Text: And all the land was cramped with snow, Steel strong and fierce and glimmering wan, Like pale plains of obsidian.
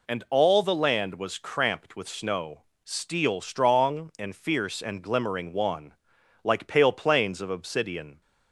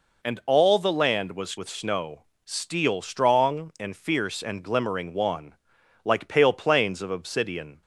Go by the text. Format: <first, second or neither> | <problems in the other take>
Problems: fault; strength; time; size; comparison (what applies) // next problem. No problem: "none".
first | skips "cramped"; at 1.5 s